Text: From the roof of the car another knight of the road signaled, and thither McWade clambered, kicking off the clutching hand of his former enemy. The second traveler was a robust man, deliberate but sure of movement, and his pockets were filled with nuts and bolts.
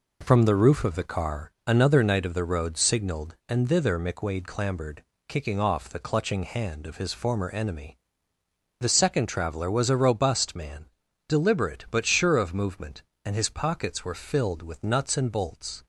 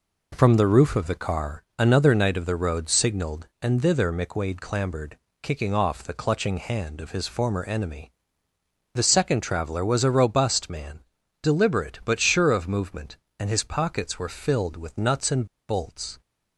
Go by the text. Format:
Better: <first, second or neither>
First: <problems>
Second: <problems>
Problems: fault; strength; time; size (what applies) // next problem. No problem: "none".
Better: first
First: none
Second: pauses between "and" and "bolts"; slight; at 15.4 s; 0.23 s long